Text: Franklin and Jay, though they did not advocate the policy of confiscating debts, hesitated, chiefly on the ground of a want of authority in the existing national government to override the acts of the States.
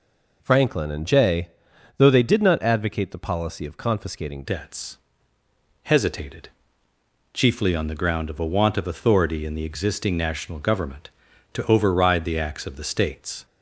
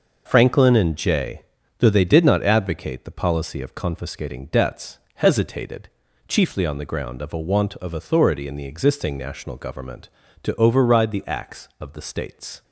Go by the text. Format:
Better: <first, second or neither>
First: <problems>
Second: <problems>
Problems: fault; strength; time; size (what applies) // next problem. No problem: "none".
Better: second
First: changes voice at "debts"; from 4.4 s on; 9.0 s long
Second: none